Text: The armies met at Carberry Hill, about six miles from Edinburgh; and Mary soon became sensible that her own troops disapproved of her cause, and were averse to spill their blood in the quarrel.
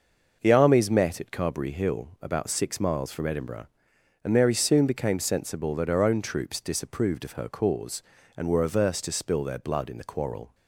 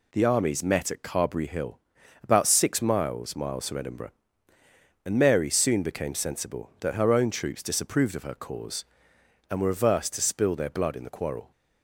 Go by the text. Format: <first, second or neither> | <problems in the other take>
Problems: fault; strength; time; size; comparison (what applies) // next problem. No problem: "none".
first | says "miles" twice; at 3.3 s